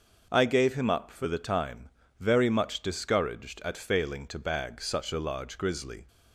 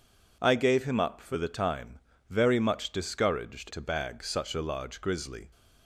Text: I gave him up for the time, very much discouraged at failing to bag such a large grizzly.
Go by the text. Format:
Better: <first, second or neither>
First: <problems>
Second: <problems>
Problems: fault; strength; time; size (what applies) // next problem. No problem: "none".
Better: first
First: none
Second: skips "at failing"; at 3.7 s